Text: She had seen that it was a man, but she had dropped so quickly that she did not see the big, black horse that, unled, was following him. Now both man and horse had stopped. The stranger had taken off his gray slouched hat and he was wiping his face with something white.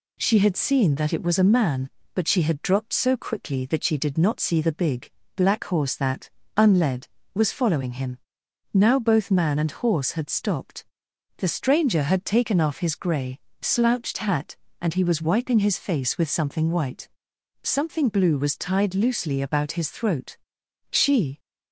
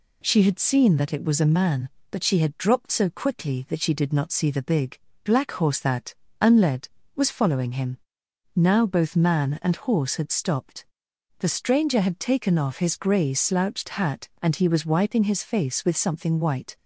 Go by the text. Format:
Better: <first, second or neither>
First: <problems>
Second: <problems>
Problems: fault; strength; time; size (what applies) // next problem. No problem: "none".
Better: second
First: pauses between "gray" and "slouched"; slight; at 13.3 s; 0.22 s long // goes on to say "Something blue was tied loosely about his throat She"; strong; from 17.6 s on; 3.7 s long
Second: none